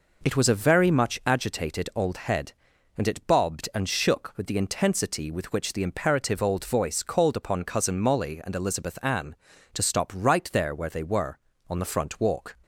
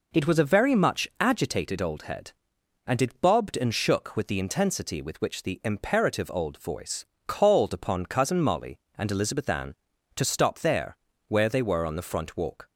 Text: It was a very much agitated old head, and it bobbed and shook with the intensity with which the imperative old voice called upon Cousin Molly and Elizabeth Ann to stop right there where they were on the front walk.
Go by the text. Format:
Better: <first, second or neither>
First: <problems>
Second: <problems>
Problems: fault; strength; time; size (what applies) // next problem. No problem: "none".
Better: first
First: none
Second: pauses between "voice" and "called"; slight; at 7.0 s; 0.22 s long // skips "right"; at 10.5 s // pauses between "there" and "where"; slight; at 10.9 s; 0.32 s long